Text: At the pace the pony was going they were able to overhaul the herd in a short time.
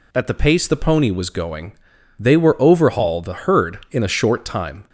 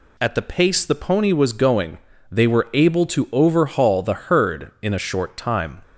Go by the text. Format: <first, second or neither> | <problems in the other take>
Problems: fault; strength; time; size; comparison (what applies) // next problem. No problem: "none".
second | pauses between "going" and "they"; noticeable; at 1.7 s; 0.48 s long; slight in the second // skips "able to"; at 2.6 s